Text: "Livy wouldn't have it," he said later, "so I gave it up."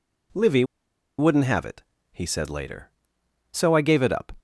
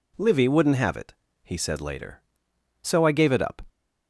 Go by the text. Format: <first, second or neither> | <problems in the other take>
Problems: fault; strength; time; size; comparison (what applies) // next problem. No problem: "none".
second | pauses between "Livy" and "wouldn't"; noticeable; at 0.6 s; 0.54 s long